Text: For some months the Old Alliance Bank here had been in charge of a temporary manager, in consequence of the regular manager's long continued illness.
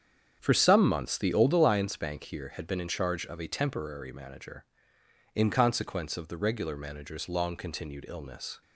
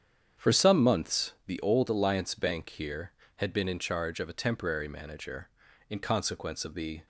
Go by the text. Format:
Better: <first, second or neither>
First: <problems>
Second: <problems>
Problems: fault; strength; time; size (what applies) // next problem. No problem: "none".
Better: first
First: starts louder than the rest; strong; until 1.4 s; 8 dB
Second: starts louder than the rest; strong; until 1.5 s; 8 dB // stops before "regular manager's long continued illness"; at 7.0 s